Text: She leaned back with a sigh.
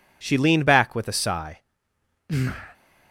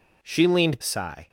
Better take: first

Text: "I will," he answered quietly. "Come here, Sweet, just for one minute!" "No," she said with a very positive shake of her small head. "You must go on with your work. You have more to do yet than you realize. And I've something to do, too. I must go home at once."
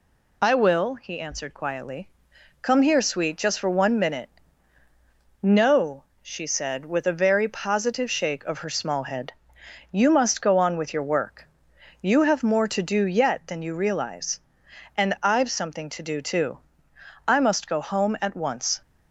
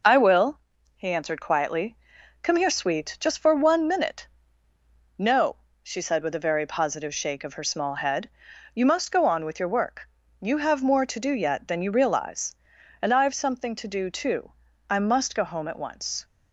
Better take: neither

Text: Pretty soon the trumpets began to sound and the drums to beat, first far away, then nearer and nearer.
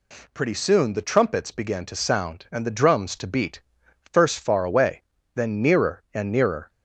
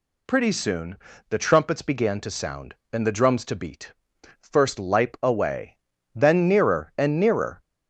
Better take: first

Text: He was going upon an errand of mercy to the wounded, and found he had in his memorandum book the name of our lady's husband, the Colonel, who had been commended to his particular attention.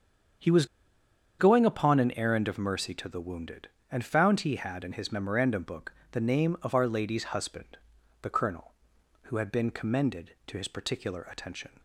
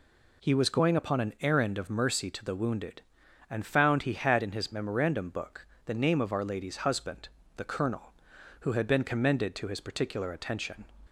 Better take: second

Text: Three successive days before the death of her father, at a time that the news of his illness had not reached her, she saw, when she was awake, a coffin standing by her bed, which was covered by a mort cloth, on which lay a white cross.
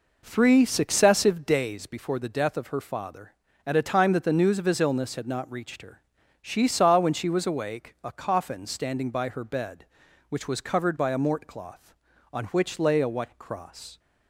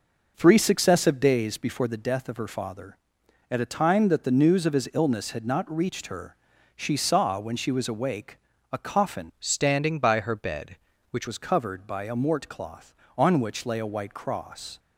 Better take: first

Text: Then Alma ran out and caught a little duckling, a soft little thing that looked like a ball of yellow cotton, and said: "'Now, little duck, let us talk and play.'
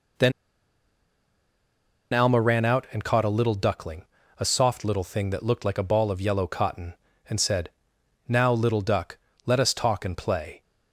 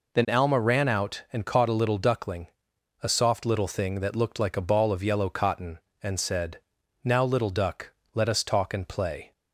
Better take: second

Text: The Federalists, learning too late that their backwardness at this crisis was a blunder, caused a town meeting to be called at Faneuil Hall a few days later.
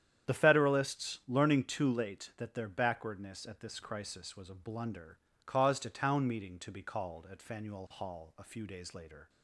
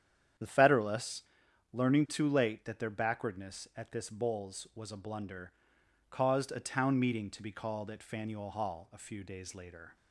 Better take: first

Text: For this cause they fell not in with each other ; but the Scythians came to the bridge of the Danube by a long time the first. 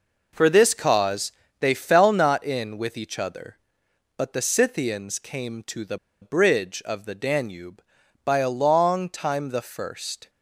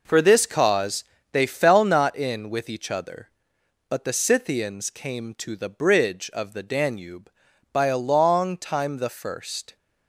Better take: second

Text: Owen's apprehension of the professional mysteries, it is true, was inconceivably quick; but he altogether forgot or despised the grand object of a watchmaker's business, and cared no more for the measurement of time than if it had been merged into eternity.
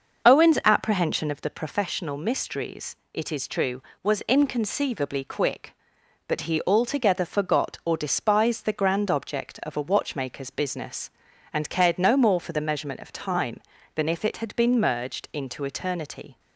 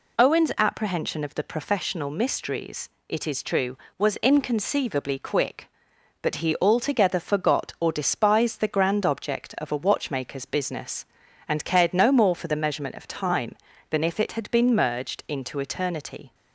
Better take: second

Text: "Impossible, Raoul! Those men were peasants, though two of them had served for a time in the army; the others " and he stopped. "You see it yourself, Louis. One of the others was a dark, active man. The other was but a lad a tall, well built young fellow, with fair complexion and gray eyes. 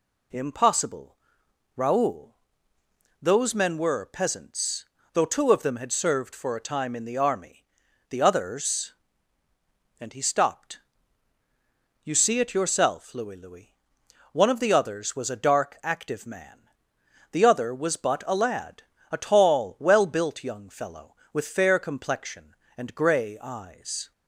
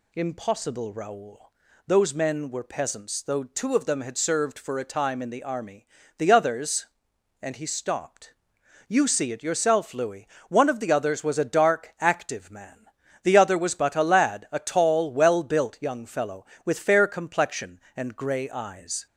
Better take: second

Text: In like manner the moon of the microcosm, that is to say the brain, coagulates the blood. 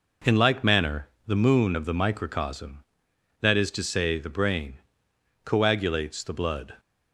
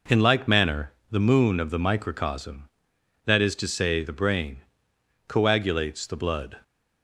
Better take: neither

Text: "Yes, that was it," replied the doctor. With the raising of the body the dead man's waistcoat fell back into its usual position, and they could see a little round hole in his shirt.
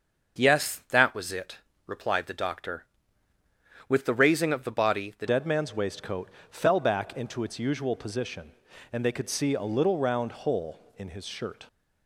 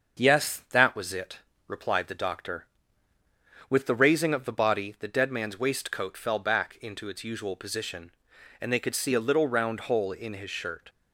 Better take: second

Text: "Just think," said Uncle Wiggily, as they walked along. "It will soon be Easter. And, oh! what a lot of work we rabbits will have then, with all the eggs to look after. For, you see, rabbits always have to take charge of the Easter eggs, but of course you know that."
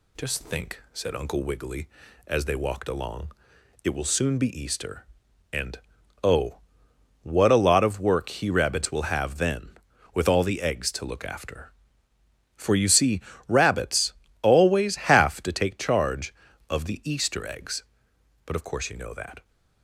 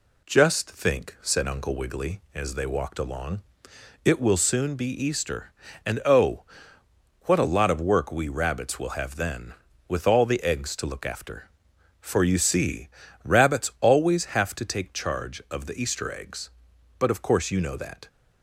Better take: second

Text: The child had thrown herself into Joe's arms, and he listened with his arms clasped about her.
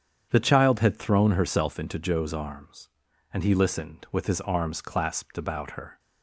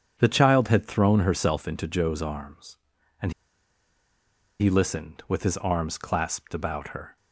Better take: first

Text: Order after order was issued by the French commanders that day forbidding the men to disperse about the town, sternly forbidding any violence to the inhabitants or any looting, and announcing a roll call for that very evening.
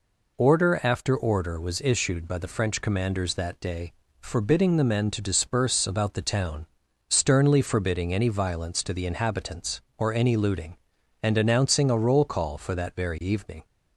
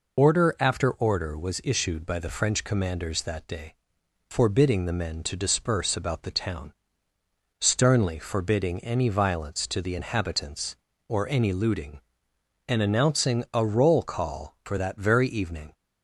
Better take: first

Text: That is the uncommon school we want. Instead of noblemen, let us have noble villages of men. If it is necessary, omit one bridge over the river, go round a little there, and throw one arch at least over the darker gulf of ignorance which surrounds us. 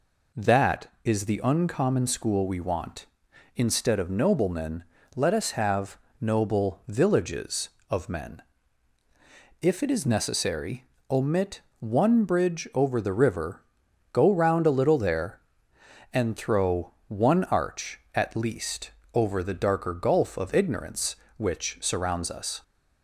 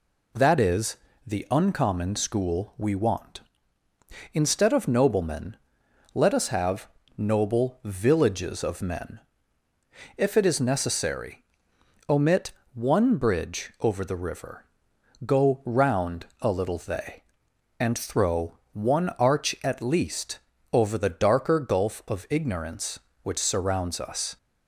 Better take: first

